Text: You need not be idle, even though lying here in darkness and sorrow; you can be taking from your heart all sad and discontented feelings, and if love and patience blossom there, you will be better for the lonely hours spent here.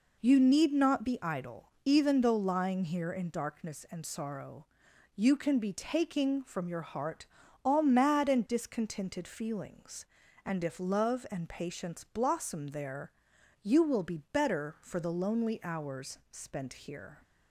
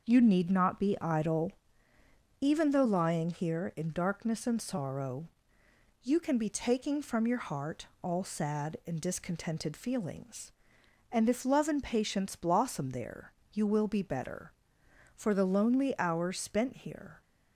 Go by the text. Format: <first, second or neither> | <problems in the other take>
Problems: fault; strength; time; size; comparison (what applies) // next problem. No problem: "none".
second | pauses between "heart" and "all"; at 7.2 s; 0.38 s long; slight in the second // says "mad" for "sad"; at 7.8 s